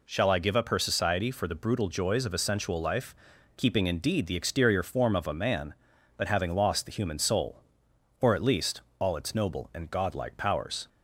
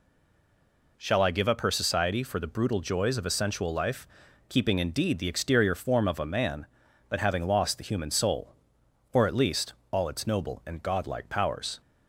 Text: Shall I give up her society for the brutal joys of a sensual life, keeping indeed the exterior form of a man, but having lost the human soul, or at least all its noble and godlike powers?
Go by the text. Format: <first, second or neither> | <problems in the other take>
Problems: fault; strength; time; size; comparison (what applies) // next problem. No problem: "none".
first | stays silent before the first word; until 0.9 s; 0.9 s long // pauses between "least" and "all"; slight; at 9.7 s; 0.18 s long; slight in the first